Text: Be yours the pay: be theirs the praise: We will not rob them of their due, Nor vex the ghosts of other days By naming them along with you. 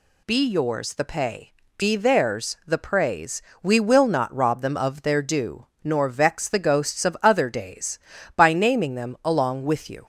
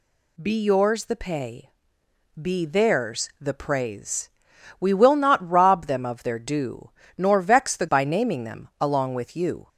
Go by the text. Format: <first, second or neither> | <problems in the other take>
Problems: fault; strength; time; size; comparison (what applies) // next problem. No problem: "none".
first | skips "ghosts of other days"; at 7.8 s